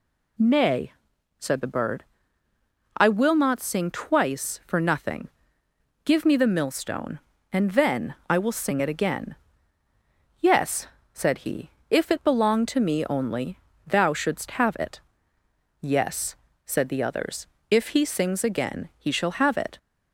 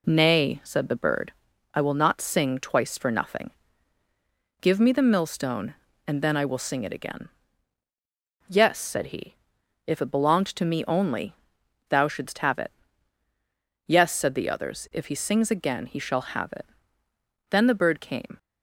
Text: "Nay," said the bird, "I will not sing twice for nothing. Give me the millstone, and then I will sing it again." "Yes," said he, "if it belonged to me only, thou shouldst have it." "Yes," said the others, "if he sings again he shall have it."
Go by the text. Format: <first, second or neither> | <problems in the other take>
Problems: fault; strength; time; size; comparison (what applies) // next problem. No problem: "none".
first | goes on to say "Then the bird came"; noticeable; from 17.4 s on; 0.88 s long